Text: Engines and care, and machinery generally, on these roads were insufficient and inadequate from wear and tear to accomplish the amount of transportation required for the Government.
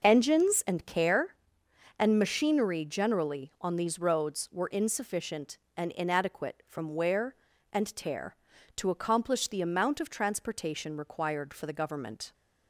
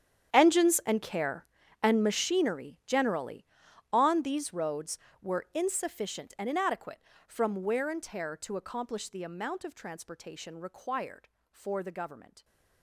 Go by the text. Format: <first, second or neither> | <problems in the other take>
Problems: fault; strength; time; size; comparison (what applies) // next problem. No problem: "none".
first | gets quieter; strong; throughout; 19.5 dB